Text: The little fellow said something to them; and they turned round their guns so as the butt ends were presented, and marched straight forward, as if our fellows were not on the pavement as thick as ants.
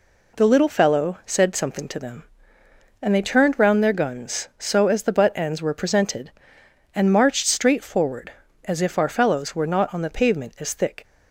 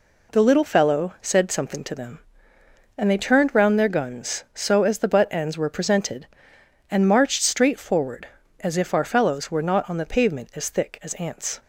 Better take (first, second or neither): second